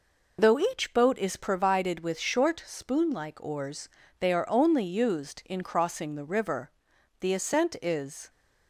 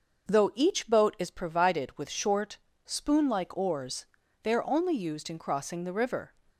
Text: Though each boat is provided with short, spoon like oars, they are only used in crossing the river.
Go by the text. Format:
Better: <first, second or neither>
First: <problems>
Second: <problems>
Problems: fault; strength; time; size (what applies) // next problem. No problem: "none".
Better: second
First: goes on to say "The ascent is"; noticeable; from 7.1 s on; 1.1 s long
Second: none